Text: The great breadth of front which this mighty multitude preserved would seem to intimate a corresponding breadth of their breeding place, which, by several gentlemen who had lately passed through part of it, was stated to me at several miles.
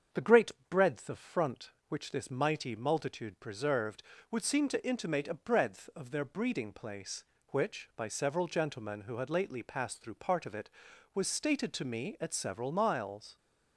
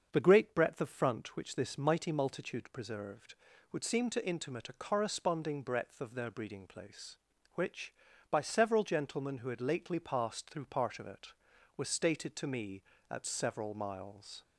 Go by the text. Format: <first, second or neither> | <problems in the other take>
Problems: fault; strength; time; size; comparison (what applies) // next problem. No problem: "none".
second | starts louder than the rest; strong; until 1.3 s; 7.5 dB; also in the second // pauses between "great" and "breadth"; slight; at 0.5 s; 0.18 s long // skips "corresponding"; at 5.3 s